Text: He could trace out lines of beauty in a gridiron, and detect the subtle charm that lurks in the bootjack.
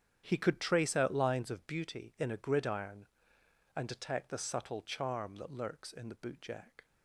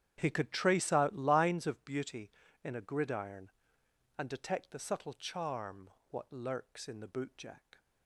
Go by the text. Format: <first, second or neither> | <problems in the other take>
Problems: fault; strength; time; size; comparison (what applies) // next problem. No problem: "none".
first | starts louder than the rest; strong; until 1.1 s; 9.5 dB; strong in the first // says "what" for "that"; at 6.1 s